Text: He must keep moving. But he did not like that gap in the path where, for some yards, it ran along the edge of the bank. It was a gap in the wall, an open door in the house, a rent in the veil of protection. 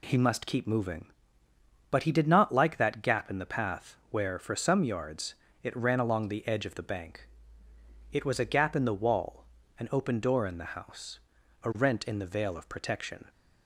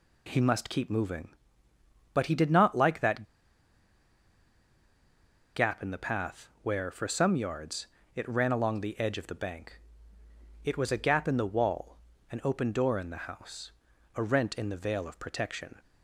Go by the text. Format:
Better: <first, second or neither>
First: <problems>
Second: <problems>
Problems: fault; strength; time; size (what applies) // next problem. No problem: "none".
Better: first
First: none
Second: pauses between "that" and "gap"; strong; at 3.2 s; 2.3 s long